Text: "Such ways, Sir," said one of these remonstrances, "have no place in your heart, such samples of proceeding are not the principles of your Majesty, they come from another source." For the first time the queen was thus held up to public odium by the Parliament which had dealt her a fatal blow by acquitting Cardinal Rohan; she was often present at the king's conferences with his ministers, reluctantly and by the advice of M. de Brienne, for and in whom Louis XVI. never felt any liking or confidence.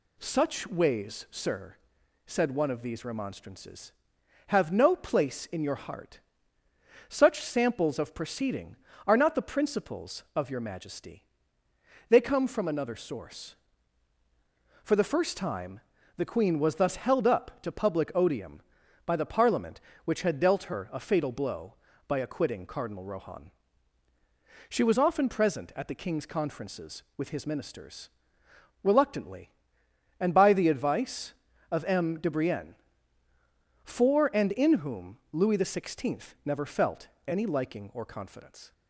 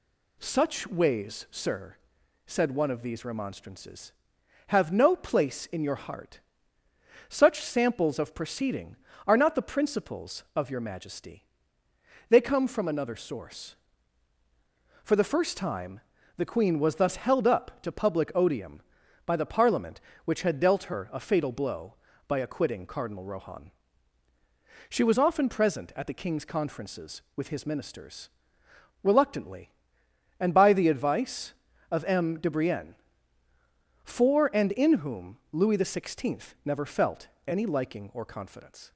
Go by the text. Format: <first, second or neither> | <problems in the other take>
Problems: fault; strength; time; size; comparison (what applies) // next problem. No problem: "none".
neither | pauses between "time" and "the"; the same in both // pauses between "felt" and "any"; slight; the same in both